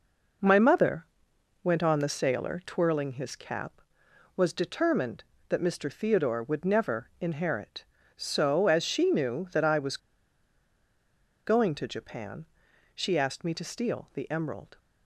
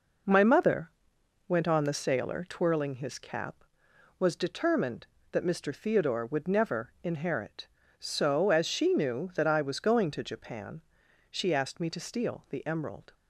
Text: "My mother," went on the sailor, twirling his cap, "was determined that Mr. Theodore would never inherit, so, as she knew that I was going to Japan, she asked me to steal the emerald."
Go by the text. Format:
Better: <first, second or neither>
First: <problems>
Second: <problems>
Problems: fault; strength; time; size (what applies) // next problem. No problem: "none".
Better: second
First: pauses between "was" and "going"; strong; at 9.9 s; 1.4 s long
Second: none